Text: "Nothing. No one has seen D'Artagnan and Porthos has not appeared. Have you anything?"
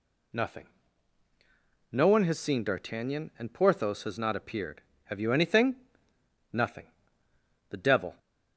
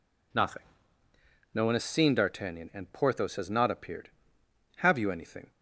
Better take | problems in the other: second | goes on to say "Nothing The devil"; from 6.5 s on; 1.6 s long

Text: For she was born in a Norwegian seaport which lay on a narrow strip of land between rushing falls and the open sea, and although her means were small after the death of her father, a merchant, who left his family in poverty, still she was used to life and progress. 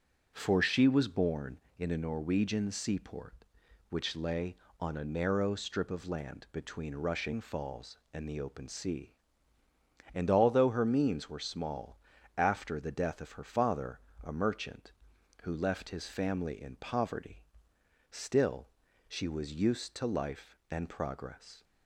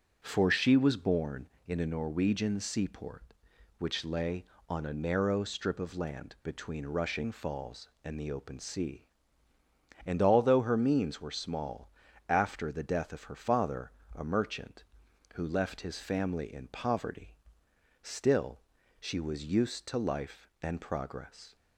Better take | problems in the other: neither | starts louder than the rest; the same in both // pauses between "small" and "after"; slight; the same in both // pauses between "still" and "she"; the same in both

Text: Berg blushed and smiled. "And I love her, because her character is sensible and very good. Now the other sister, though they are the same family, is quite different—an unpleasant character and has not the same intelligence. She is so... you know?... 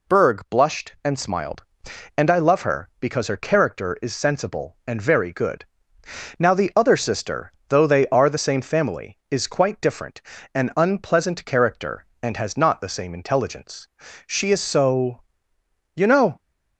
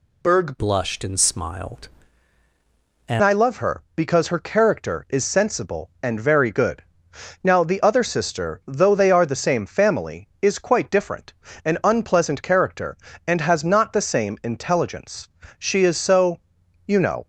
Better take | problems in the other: first | changes voice from "blushed" to "And"; from 0.5 to 3.2 s; 2.7 s long

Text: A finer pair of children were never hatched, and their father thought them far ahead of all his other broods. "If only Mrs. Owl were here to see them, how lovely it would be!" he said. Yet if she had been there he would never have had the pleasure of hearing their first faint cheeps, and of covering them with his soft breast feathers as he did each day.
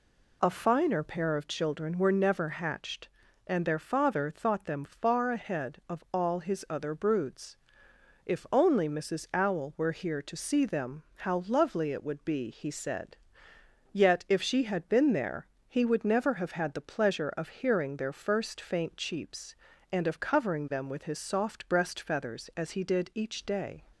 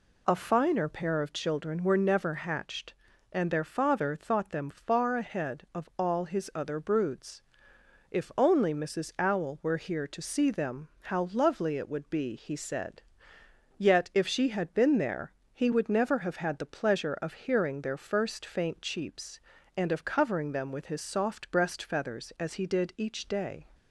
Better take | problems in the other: neither | pauses between "there" and "he"; slight; the same in both

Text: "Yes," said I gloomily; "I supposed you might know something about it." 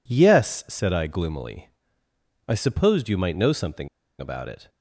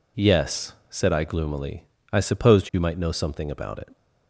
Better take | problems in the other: second | pauses between "something" and "about"; slight; at 3.8 s; 0.32 s long

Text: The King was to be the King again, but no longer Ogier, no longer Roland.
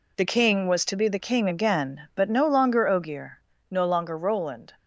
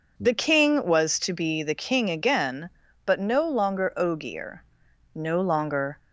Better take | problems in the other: first | stops before "Roland"; at 5.9 s

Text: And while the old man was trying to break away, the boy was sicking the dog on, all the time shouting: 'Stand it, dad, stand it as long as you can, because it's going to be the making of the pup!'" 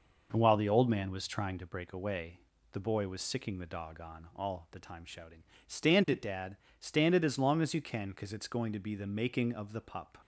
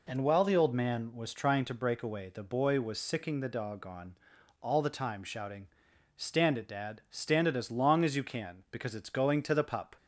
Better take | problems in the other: first | skips "be the making of"; at 9.5 s

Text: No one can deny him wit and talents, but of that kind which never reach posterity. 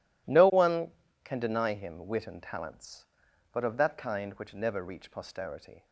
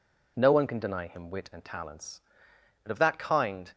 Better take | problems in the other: first | stops before "which never reach posterity"; at 3.7 s

